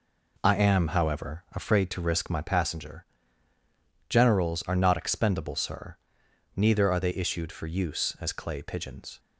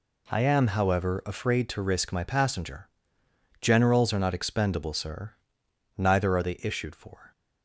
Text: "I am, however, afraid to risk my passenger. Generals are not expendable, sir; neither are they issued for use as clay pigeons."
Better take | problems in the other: first | stops before "use as clay pigeons"; at 7.3 s

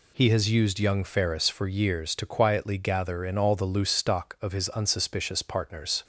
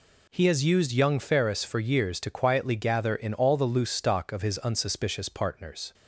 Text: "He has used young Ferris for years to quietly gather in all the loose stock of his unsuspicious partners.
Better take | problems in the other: neither | none

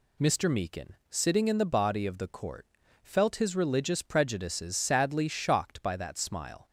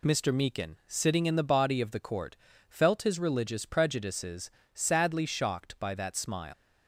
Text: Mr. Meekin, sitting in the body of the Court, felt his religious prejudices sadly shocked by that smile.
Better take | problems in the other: first | pauses between "prejudices" and "sadly"; slight; at 4.5 s; 0.24 s long // leaves "smile" unfinished; at 6.5 s; 145 ms

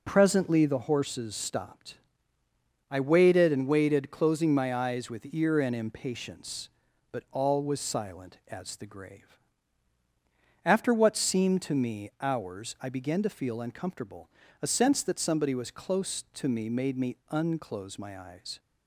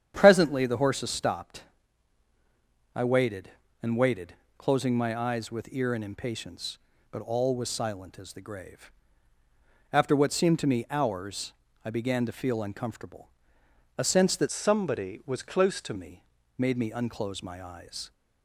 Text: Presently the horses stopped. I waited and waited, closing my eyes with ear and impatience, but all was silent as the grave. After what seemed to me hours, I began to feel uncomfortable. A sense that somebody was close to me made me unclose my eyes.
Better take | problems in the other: first | starts louder than the rest; strong; until 1.1 s; 9 dB // changes voice from "somebody" to "to"; from 14.4 to 15.9 s; 1.5 s long // pauses between "me" and "made"; slight; at 16.2 s; 0.36 s long

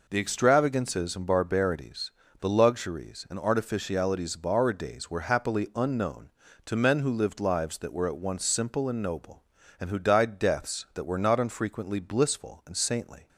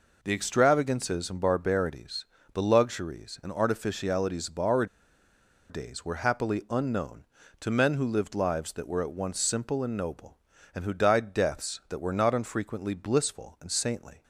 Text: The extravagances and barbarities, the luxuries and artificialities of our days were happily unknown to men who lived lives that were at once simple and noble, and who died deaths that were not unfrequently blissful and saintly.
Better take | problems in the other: first | pauses between "our" and "days"; noticeable; at 4.8 s; 0.84 s long

